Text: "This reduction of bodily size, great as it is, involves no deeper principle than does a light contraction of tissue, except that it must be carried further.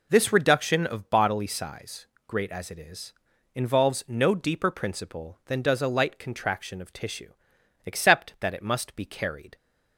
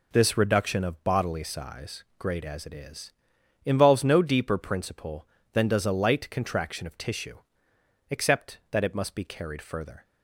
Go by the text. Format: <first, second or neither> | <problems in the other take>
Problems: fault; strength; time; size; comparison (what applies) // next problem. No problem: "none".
second | stops before "further"; at 9.5 s